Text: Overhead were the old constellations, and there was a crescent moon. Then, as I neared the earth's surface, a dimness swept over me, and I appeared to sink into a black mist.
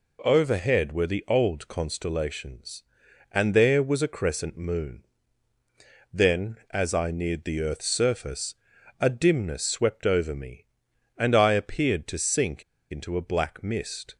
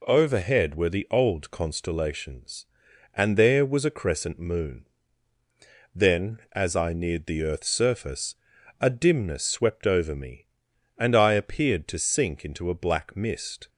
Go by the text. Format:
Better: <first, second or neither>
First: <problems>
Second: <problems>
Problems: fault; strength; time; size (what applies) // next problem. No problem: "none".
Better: second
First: pauses between "sink" and "into"; slight; at 12.6 s; 0.28 s long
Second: none